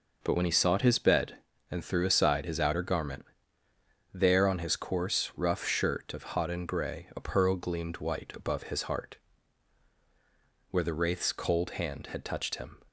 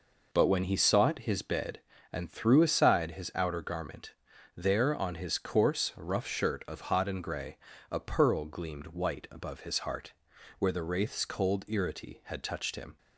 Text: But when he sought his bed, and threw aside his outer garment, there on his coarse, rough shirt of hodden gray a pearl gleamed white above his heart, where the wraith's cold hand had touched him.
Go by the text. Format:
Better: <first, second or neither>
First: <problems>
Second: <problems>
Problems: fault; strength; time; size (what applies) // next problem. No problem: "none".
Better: first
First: none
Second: pauses between "gray" and "a"; slight; at 7.5 s; 0.32 s long // says "irity" for "hand"; at 11.6 s